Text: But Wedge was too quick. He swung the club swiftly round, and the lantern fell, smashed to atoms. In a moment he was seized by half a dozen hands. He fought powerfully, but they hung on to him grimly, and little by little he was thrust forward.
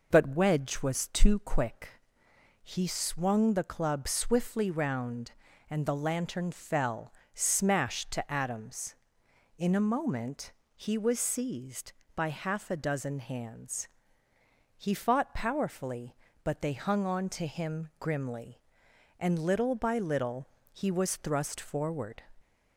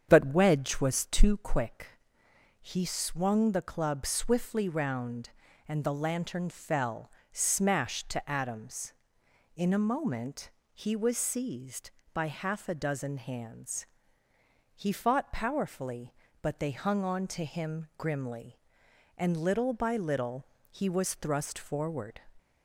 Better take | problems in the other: first | starts louder than the rest; strong; until 1.3 s; 8 dB // pauses between "moment" and "he"; slight; at 10.4 s; 0.24 s long; slight in the first // pauses between "little" and "he"; slight; at 20.4 s; 0.28 s long; slight in the first

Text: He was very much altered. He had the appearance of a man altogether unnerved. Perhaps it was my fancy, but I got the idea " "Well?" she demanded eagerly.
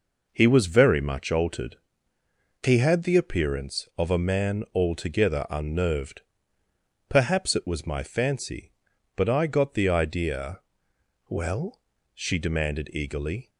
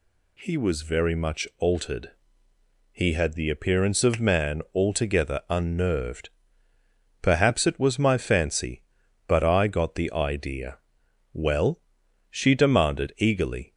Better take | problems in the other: first | skips "a"; at 4.1 s

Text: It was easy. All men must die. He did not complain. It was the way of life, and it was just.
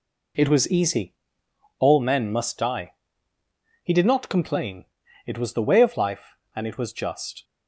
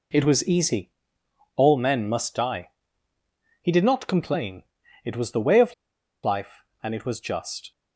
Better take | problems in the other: first | pauses between "of" and "life"; noticeable; at 5.7 s; 0.49 s long

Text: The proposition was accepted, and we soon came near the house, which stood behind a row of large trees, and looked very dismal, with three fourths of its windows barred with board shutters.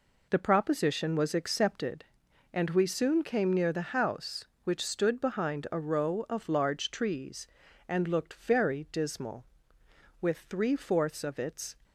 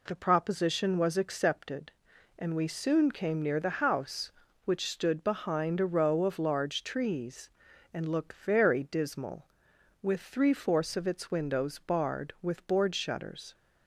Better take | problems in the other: second | stops before "windows barred with board shutters"; at 11.8 s

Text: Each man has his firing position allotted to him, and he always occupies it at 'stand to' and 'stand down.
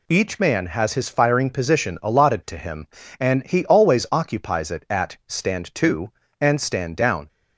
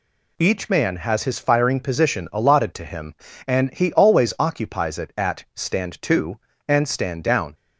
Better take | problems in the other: neither | none

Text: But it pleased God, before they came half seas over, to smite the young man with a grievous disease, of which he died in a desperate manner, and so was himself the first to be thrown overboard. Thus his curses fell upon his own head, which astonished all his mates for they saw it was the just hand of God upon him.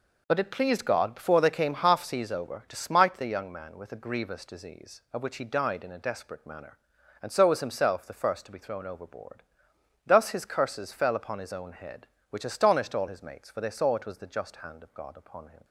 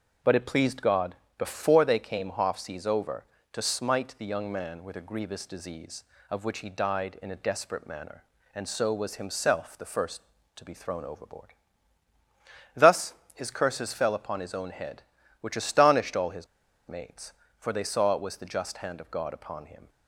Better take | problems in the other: first | starts louder than the rest; until 1.4 s; 7 dB // pauses between "Thus" and "his"; slight; at 13.1 s; 0.20 s long // pauses between "his" and "mates"; at 16.4 s; 0.40 s long

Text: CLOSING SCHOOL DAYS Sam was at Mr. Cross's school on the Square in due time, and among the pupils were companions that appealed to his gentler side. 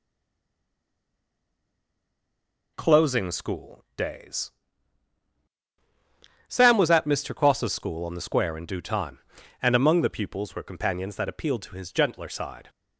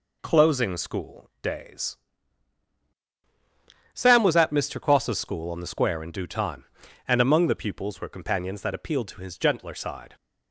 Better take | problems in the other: second | stays silent before the first word; strong; until 2.7 s; 2.7 s long // pauses between "DAYS" and "Sam"; strong; at 4.4 s; 1.9 s long; strong in the second

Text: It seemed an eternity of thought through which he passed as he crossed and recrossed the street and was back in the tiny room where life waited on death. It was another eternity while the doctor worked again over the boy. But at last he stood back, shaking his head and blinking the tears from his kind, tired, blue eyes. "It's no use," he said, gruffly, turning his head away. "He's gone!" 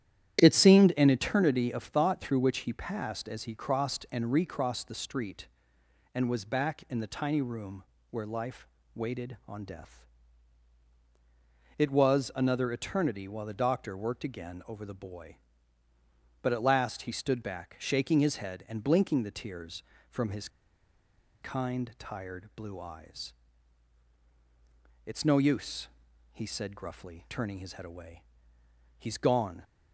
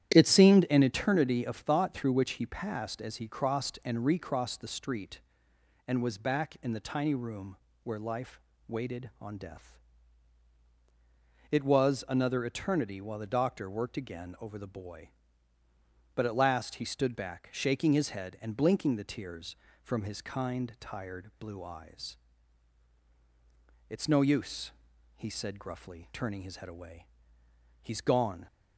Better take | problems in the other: second | starts louder than the rest; strong; until 1.4 s; 11 dB; strong in the second // pauses between "room" and "where"; slight; at 7.8 s; 0.26 s long; slight in the second // pauses between "life" and "waited"; slight; at 8.6 s; 0.30 s long; slight in the second // pauses between "his" and "kind"; noticeable; at 20.4 s; 0.94 s long

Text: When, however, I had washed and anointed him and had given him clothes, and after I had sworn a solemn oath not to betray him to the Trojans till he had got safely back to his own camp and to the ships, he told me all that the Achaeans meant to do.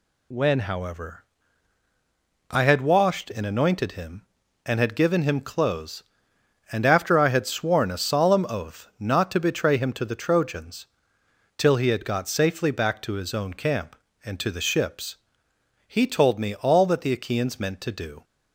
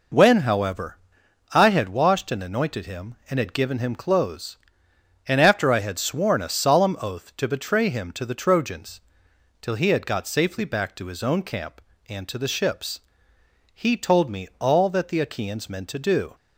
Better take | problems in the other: first | skips "not"; at 7.3 s // pauses between "Trojans" and "till"; noticeable; at 9.0 s; 0.62 s long; noticeable in the first

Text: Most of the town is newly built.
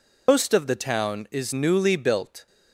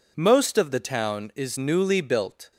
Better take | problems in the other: second | loses the start of "Most"; at 0.2 s; 165 ms

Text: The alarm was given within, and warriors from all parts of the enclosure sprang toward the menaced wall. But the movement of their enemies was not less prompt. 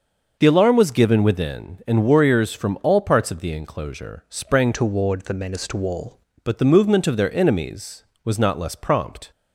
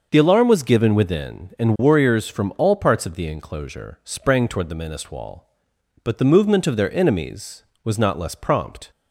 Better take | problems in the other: second | starts louder than the rest; noticeable; until 1.4 s; 6 dB; also in the second // changes voice from "toward" to "wall"; from 4.7 to 6.1 s; 1.4 s long

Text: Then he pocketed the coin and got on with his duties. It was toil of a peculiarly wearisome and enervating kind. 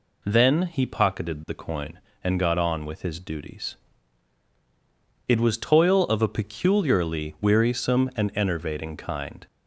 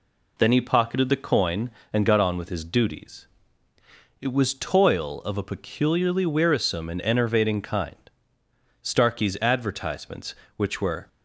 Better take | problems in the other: first | goes on to say "Starkey's advertisements which were"; strong; from 8.8 s on; 2.2 s long

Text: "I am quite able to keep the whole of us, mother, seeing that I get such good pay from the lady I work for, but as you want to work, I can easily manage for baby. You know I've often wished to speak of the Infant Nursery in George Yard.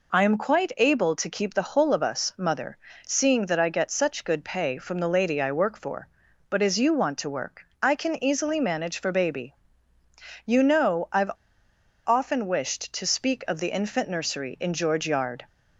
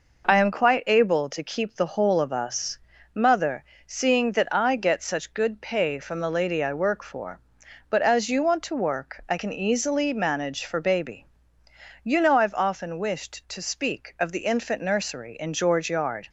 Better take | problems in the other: second | pauses between "I've" and "often"; noticeable; at 11.3 s; 0.75 s long

